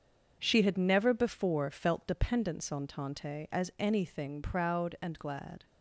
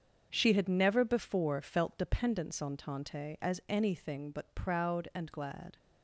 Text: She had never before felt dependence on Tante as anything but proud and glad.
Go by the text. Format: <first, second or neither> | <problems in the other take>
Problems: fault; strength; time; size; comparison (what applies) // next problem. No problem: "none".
second | starts louder than the rest; until 1.4 s; 7 dB; strong in the second // skips "but"; at 4.4 s